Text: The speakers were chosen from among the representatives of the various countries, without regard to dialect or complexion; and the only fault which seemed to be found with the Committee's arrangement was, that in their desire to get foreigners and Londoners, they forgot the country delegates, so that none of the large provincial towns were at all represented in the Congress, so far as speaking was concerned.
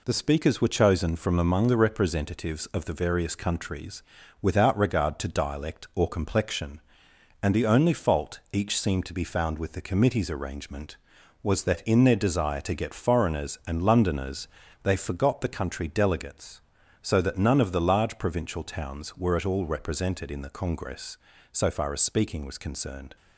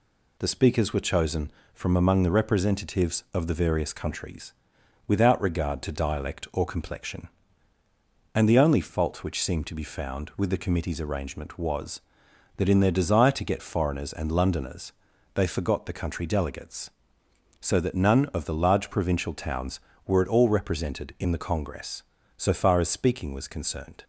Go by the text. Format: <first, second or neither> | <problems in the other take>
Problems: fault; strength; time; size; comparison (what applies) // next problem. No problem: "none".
second | says "each" for "which"; at 8.5 s